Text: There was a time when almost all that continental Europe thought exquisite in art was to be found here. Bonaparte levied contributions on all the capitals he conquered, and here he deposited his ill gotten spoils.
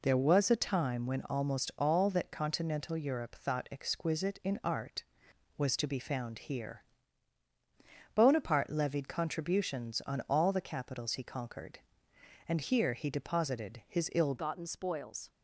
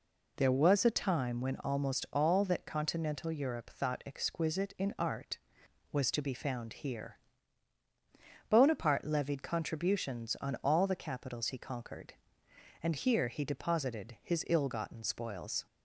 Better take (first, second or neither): second